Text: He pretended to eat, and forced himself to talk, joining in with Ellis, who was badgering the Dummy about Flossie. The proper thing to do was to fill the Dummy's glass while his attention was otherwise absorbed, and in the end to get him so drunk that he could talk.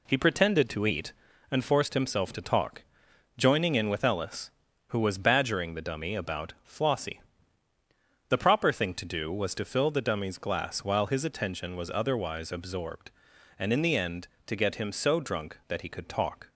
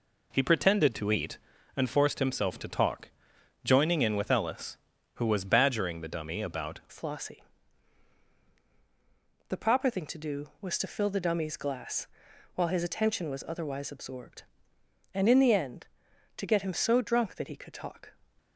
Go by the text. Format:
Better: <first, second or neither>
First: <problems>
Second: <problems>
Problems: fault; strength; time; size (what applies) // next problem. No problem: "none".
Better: first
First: none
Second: changes voice at "Flossie"; from 6.9 s on; 11.2 s long // pauses between "glass" and "while"; noticeable; at 12.0 s; 0.48 s long